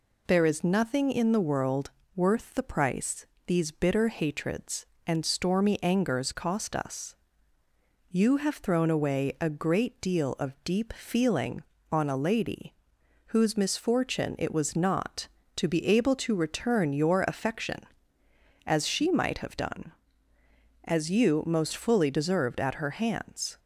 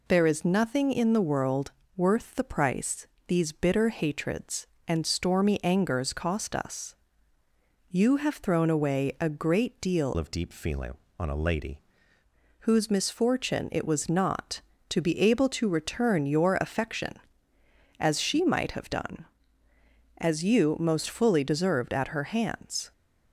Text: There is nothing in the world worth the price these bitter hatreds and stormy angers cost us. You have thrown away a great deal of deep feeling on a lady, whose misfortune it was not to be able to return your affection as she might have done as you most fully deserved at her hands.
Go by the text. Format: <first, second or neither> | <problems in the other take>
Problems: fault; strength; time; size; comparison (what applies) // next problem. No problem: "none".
first | pauses between "world" and "worth"; slight; at 1.7 s; 0.24 s long; slight in the first // pauses between "price" and "these"; slight; at 3.0 s; 0.20 s long; slight in the first // changes voice from "of" to "lady"; from 10.1 to 11.8 s; 1.7 s long